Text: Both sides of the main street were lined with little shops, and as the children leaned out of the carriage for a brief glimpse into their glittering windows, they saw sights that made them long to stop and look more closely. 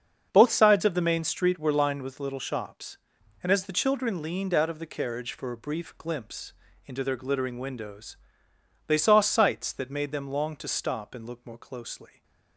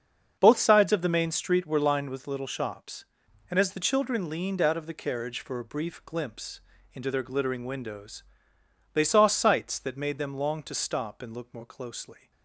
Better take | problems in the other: neither | starts louder than the rest; the same in both // pauses between "glimpse" and "into"; slight; the same in both

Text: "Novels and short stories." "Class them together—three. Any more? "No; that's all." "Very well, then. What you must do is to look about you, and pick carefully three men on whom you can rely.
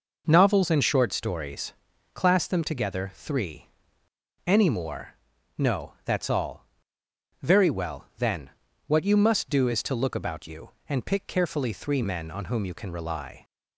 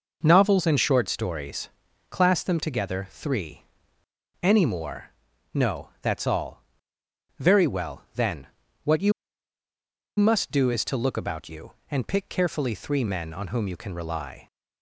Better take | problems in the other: first | pauses between "you" and "must"; at 9.1 s; 1.0 s long

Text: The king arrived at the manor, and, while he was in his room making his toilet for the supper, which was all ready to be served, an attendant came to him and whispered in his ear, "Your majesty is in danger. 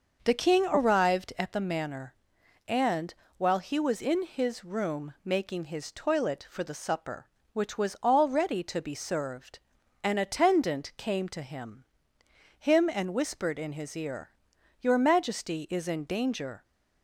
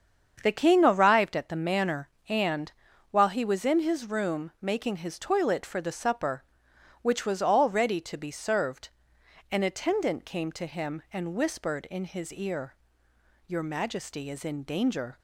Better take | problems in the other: second | starts louder than the rest; noticeable; until 1.2 s; 6 dB; strong in the second // says "him" twice; at 12.5 s

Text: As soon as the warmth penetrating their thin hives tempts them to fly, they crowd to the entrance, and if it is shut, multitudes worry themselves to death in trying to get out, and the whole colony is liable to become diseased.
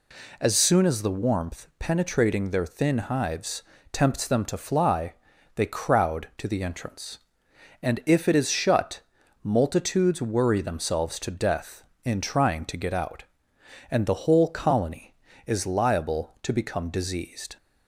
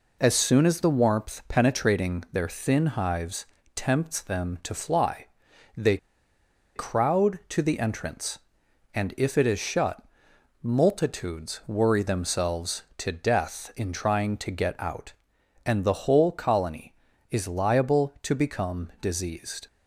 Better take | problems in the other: first | pauses between "hives" and "tempts"; slight; at 3.4 s; 0.30 s long; slight in the first // pauses between "they" and "crowd"; noticeable; at 5.9 s; 0.79 s long

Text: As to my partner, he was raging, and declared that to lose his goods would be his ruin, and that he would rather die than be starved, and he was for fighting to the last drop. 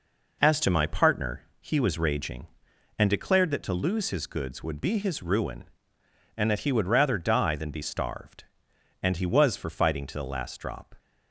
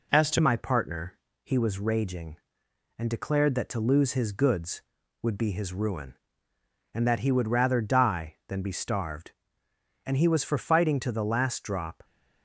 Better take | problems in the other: first | changes voice at "my"; from 0.4 s on; 11.6 s long

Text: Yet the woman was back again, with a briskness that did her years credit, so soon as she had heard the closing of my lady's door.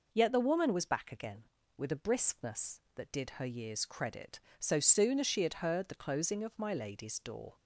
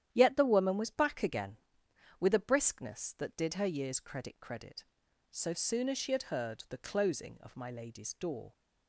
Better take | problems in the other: first | starts louder than the rest; strong; until 1.1 s; 10.5 dB // says "credit" twice; at 4.4 s

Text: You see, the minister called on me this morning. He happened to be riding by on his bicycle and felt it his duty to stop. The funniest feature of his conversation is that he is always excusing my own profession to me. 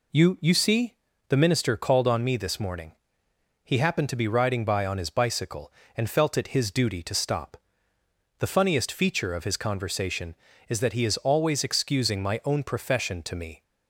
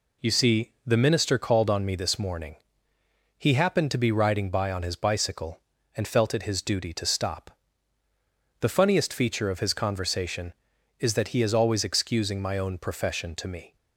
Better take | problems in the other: second | says "You" twice; at 0.4 s

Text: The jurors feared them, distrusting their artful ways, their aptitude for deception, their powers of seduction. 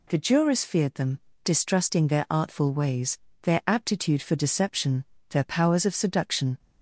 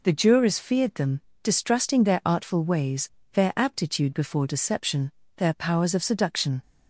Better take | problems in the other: first | says "before" for "for"; at 4.1 s

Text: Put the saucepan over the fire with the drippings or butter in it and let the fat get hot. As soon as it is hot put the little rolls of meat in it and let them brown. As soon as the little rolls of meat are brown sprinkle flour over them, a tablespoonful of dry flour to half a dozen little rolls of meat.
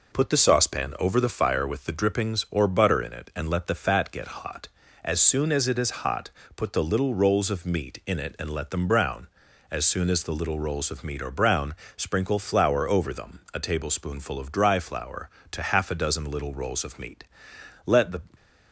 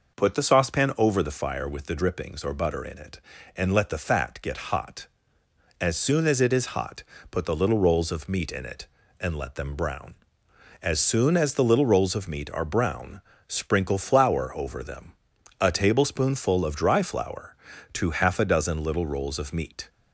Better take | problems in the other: second | pauses between "hot" and "put"; slight; at 6.2 s; 0.26 s long; slight in the second // pauses between "brown" and "sprinkle"; slight; at 11.7 s; 0.24 s long; slight in the second // goes on to say "Let the"; slight; from 17.8 s on; 0.34 s long

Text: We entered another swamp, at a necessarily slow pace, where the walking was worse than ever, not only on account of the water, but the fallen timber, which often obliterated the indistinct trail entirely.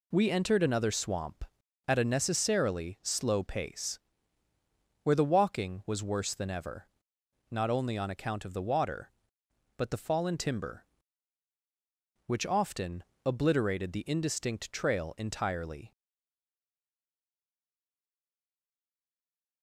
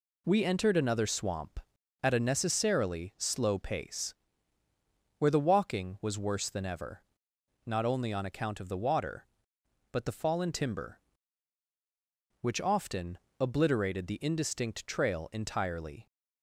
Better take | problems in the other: second | pauses between "often" and "obliterated"; slight; at 13.0 s; 0.20 s long; slight in the second // stays silent after the last word; strong; from 15.9 s on; 3.7 s long

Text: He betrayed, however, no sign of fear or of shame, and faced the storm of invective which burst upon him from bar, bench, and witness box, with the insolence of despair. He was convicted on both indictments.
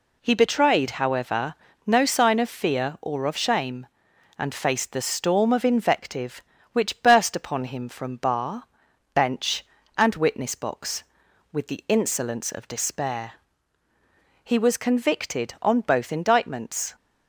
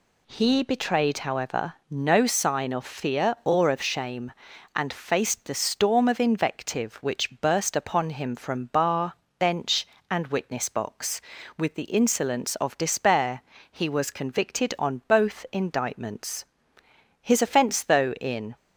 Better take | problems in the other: first | goes on to say "His offence though in"; from 17.2 s on; 1.3 s long

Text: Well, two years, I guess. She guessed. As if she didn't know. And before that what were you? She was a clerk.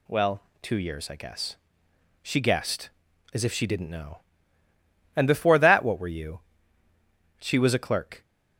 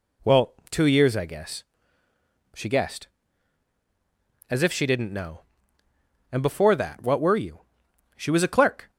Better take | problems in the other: neither | none

